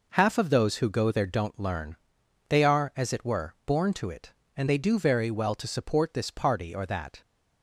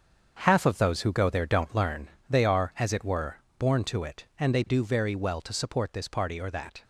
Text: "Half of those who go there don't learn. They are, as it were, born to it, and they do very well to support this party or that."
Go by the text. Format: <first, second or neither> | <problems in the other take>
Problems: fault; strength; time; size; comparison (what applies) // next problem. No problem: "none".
first | gets quieter; strong; throughout; 9.5 dB